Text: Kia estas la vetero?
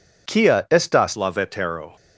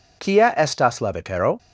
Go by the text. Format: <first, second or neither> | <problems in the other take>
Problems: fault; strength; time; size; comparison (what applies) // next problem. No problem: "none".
second | pauses between "Kia" and "estas"; slight; at 0.5 s; 0.22 s long; slight in the second // changes voice at "la"; from 1.1 s on; 0.8 s long